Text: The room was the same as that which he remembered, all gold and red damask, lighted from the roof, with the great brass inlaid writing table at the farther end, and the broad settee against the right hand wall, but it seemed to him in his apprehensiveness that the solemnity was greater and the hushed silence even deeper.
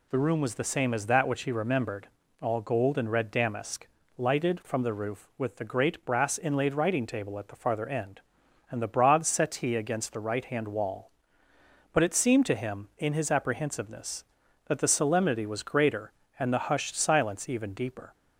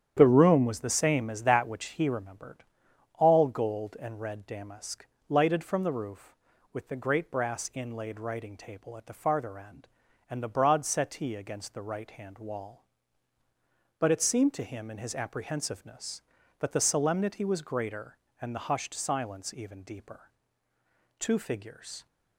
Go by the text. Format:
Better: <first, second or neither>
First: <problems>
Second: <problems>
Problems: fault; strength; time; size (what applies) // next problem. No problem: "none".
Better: first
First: none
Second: starts louder than the rest; strong; until 1.1 s; 9 dB // goes on to say "Two figures"; noticeable; from 21.1 s on; 0.88 s long